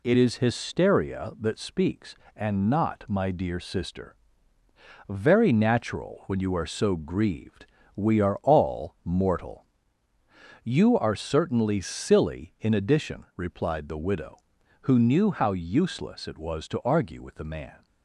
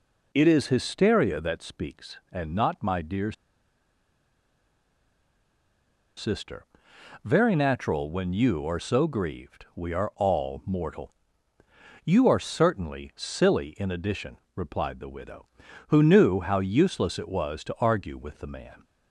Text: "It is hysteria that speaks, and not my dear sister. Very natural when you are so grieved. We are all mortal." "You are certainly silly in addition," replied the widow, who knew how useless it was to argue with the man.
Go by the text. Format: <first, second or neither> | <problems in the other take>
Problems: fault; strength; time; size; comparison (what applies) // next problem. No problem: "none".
first | pauses between "dear" and "sister"; strong; at 3.3 s; 2.8 s long